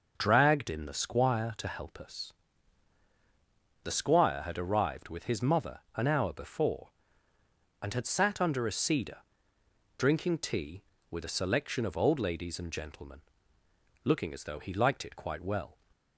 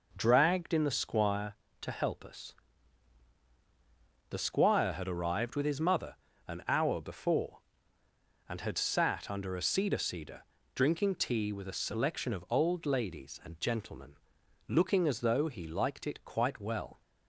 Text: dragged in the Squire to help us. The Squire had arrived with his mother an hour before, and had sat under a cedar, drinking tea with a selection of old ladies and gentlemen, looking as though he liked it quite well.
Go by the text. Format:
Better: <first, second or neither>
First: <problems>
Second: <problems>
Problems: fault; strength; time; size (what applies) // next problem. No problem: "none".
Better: first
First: pauses between "mother" and "an"; slight; at 5.7 s; 0.16 s long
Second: pauses between "mother" and "an"; slight; at 6.1 s; 0.32 s long // says "cedar" twice; at 9.9 s